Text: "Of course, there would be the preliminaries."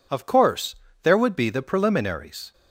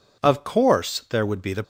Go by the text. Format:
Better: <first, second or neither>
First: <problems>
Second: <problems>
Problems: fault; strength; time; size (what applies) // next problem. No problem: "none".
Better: first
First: none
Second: stops before "preliminaries"; at 1.6 s